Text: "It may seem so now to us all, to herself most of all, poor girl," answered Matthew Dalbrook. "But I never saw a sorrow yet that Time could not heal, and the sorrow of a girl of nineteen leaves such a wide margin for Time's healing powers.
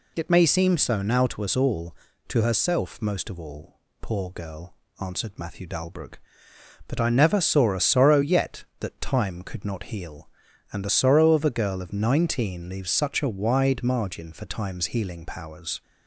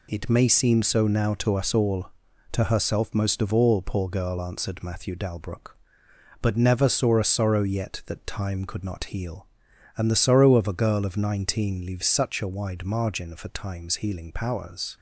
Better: first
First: none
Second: skips "I"; at 6.5 s

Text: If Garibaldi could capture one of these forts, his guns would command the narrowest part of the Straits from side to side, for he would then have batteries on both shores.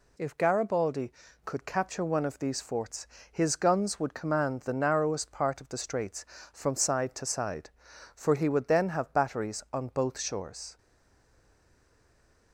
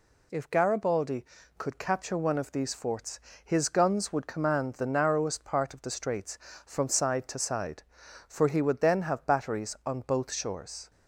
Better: second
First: stays silent after the last word; noticeable; from 10.7 s on; 1.8 s long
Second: none

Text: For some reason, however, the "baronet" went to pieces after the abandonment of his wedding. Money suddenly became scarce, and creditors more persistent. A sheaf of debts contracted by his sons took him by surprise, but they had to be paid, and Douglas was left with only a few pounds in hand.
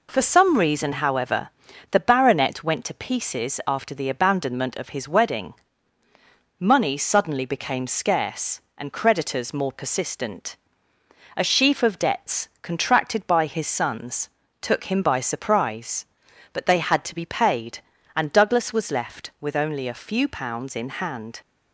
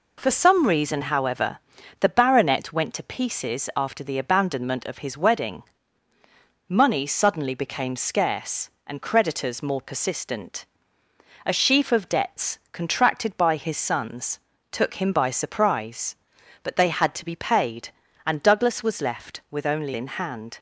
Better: first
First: pauses between "sons" and "took"; slight; at 14.3 s; 0.32 s long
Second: pauses between "sons" and "took"; slight; at 14.4 s; 0.32 s long // skips "a few pounds"; at 19.9 s

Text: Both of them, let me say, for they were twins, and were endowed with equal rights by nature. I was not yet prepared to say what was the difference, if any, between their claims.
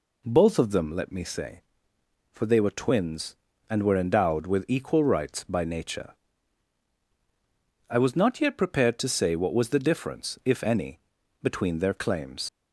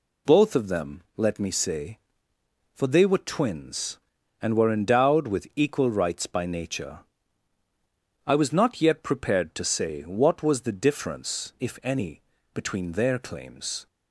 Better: second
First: leaves "claims" unfinished; at 12.4 s; 85 ms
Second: none

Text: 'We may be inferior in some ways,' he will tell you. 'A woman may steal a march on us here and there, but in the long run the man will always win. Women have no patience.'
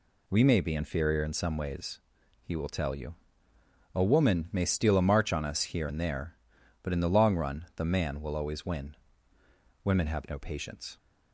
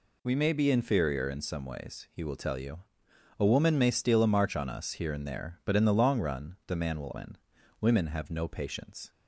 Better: first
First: none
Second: skips "always"; at 7.1 s

